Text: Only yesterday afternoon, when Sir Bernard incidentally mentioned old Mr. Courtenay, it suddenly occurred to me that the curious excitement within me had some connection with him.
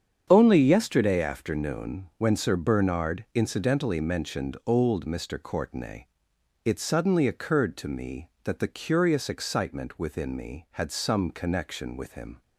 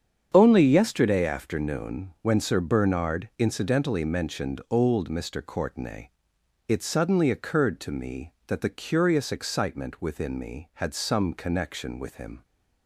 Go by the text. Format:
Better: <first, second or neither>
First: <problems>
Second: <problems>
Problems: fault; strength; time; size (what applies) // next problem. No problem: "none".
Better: neither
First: starts louder than the rest; strong; until 1.3 s; 7.5 dB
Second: starts louder than the rest; strong; until 1.3 s; 8 dB